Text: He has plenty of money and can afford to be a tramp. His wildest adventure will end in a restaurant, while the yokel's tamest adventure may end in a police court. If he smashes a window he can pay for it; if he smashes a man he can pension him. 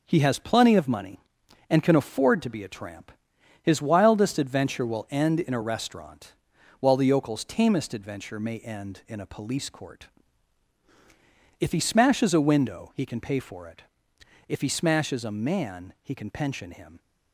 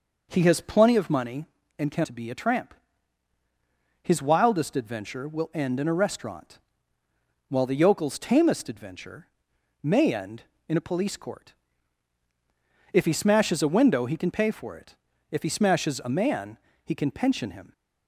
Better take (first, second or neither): first